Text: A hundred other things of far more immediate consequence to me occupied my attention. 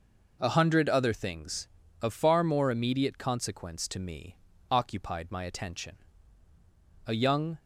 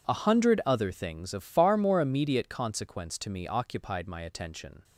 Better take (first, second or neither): second